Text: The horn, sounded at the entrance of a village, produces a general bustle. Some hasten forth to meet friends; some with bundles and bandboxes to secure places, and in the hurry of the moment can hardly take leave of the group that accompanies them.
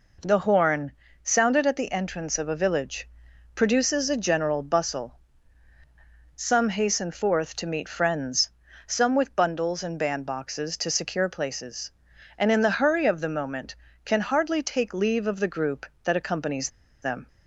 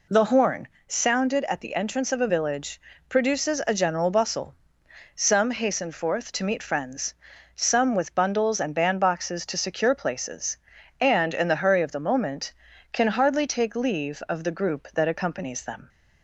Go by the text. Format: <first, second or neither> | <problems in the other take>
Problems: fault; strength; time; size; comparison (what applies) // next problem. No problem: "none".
second | pauses between "accompanies" and "them"; slight; at 16.6 s; 0.34 s long